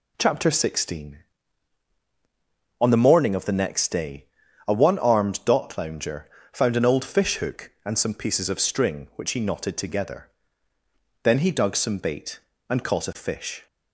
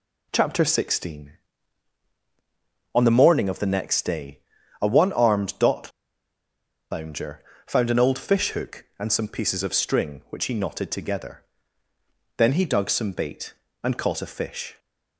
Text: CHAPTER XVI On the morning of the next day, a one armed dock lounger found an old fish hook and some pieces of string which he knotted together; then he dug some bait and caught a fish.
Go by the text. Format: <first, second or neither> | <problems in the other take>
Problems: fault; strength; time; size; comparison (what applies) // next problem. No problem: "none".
first | pauses between "dock" and "lounger"; at 5.9 s; 1.0 s long // pauses between "lounger" and "found"; slight; at 7.4 s; 0.24 s long; slight in the first